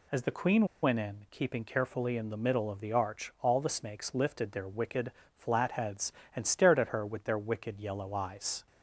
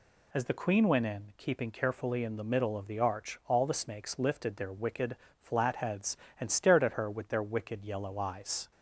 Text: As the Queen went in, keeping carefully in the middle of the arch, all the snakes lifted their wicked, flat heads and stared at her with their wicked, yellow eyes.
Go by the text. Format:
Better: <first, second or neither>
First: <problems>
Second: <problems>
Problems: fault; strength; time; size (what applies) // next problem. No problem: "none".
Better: second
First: pauses between "Queen" and "went"; slight; at 0.6 s; 0.16 s long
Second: none